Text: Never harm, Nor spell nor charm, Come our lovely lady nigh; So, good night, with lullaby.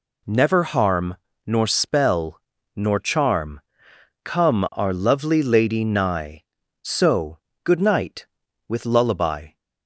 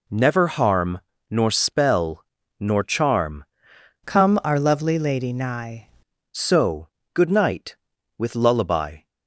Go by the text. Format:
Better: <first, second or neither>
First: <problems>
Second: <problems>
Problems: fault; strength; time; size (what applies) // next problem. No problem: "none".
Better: first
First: pauses between "spell" and "nor"; slight; at 2.3 s; 0.36 s long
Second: pauses between "spell" and "nor"; slight; at 2.2 s; 0.36 s long // changes voice from "Come" to "nigh"; from 4.0 to 5.8 s; 1.8 s long